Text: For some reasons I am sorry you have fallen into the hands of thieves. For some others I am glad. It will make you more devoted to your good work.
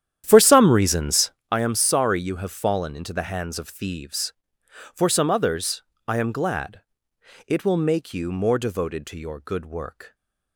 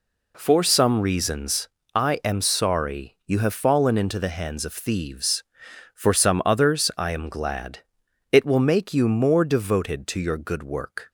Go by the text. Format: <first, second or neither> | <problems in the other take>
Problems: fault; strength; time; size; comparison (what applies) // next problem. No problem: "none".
second | starts louder than the rest; strong; until 1.5 s; 10.5 dB // pauses between "reasons" and "I"; slight; at 1.3 s; 0.20 s long; slight in the second // pauses between "others" and "I"; slight; at 5.8 s; 0.24 s long